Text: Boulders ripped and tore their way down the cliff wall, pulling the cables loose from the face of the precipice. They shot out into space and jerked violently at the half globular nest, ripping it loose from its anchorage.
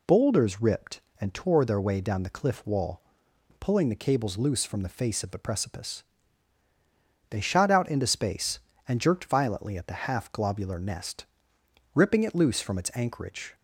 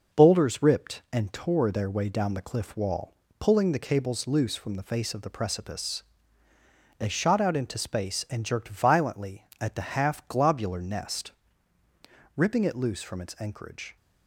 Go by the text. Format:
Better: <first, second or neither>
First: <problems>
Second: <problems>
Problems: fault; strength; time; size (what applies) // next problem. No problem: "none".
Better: first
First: none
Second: gets quieter; noticeable; throughout; 4.5 dB